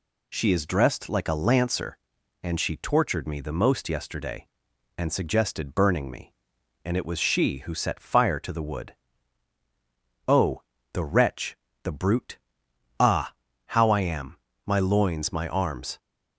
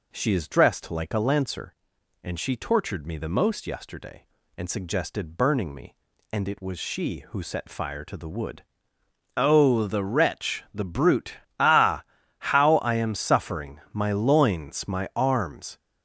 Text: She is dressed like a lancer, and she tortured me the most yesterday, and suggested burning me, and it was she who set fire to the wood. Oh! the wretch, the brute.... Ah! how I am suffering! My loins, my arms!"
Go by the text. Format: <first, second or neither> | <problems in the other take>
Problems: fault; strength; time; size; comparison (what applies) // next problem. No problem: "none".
second | skips "suffering"; at 14.5 s